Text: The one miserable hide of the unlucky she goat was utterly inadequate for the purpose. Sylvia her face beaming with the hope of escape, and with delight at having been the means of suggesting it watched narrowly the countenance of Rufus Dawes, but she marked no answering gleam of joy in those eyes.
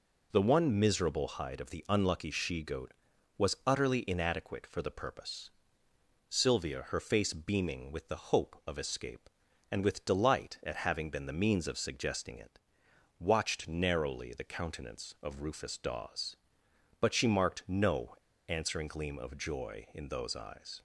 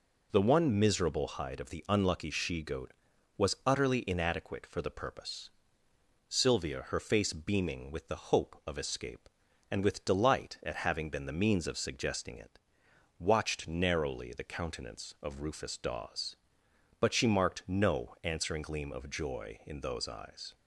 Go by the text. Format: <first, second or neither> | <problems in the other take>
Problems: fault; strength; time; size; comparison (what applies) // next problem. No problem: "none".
second | pauses between "it" and "watched"; noticeable; at 12.6 s; 0.58 s long; noticeable in the second // pauses between "no" and "answering"; slight; at 18.1 s; 0.32 s long